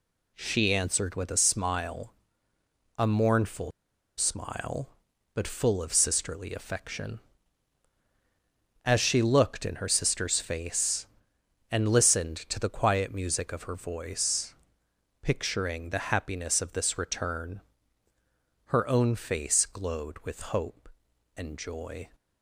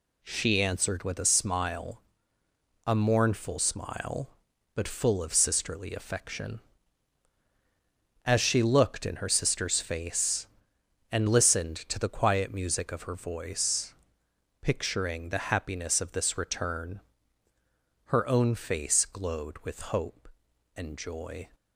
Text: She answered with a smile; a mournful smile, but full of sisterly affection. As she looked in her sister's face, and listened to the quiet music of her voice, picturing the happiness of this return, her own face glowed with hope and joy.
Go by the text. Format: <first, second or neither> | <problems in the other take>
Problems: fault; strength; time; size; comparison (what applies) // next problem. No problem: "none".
second | pauses between "mournful" and "smile"; noticeable; at 3.7 s; 0.47 s long